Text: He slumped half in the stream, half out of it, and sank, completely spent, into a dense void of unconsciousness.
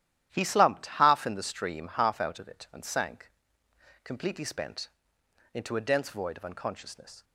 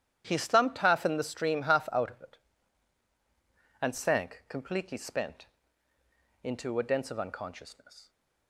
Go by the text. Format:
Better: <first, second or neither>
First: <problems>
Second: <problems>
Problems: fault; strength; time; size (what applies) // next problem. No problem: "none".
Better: first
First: starts louder than the rest; strong; until 1.3 s; 12 dB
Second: starts louder than the rest; strong; until 1.2 s; 10.5 dB // skips "void"; at 7.1 s